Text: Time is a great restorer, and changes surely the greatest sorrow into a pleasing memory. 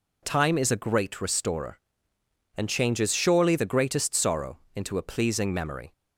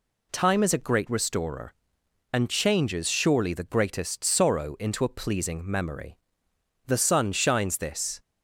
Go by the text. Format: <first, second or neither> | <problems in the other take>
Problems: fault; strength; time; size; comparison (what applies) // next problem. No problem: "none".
first | goes on to say "The sun shines this"; from 6.8 s on; 1.3 s long